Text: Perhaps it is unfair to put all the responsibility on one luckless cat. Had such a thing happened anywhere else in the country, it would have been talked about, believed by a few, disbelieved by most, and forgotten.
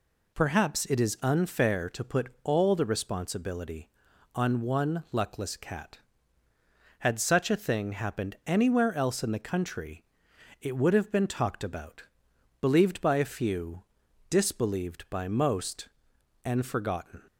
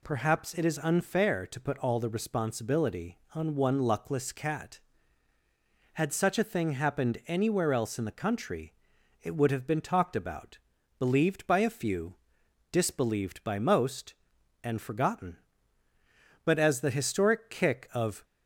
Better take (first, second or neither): first